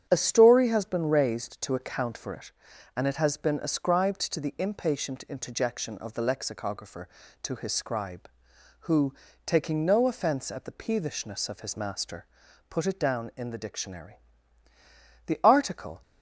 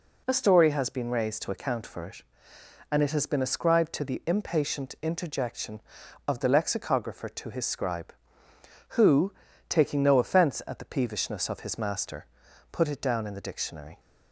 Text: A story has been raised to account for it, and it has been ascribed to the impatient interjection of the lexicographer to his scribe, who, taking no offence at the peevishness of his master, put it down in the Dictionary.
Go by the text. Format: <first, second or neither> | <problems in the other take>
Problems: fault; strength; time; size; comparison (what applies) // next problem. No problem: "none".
second | starts louder than the rest; strong; until 1.1 s; 9 dB // goes on to say "The article"; noticeable; from 15.2 s on; 0.76 s long